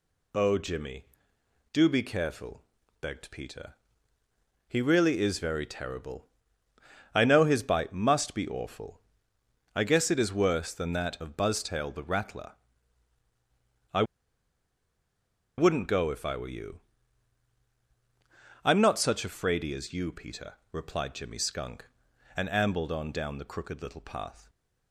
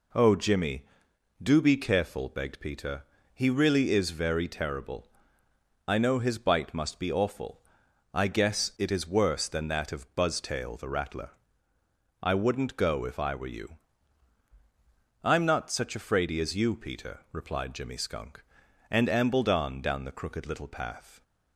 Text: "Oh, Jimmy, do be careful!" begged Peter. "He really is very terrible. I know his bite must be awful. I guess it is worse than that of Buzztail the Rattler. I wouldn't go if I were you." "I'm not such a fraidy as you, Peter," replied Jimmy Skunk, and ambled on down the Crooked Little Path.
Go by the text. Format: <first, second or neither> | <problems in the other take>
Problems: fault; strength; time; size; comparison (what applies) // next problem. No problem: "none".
second | pauses between "I" and "wouldn't"; strong; at 14.0 s; 1.5 s long